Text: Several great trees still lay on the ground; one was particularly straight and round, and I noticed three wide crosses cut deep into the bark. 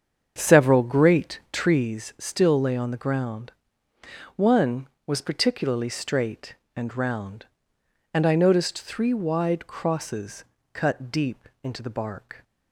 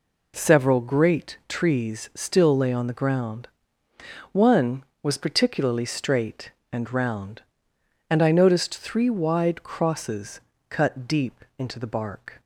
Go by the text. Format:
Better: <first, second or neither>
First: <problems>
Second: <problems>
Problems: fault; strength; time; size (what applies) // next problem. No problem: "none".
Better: second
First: starts louder than the rest; strong; until 1.9 s; 7.5 dB // pauses between "crosses" and "cut"; slight; at 10.4 s; 0.30 s long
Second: pauses between "crosses" and "cut"; slight; at 10.4 s; 0.30 s long